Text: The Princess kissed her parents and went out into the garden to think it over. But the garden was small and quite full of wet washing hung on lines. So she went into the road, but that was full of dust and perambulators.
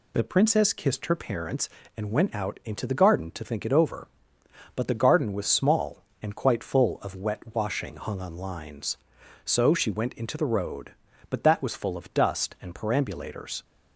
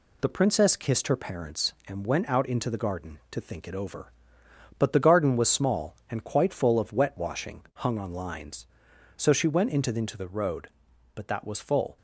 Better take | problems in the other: first | stops before "of dust and perambulators"; at 11.9 s

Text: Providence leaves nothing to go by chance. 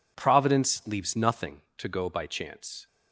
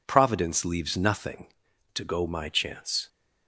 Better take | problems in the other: first | says "my" for "by"; at 2.2 s

